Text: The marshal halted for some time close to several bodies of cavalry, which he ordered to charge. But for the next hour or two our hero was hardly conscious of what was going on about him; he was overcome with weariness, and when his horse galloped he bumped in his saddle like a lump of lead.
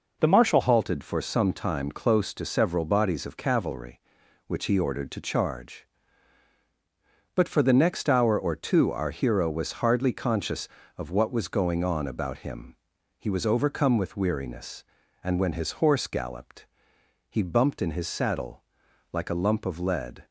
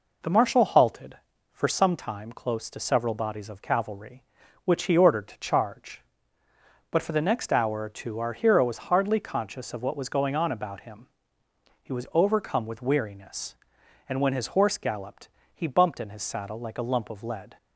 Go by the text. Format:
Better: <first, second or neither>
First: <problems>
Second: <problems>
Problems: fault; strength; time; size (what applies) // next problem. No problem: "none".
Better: second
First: changes voice at "halted"; from 0.6 s on; 19.6 s long // pauses between "galloped" and "he"; noticeable; at 16.6 s; 0.64 s long // pauses between "saddle" and "like"; noticeable; at 18.6 s; 0.50 s long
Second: pauses between "galloped" and "he"; slight; at 15.2 s; 0.26 s long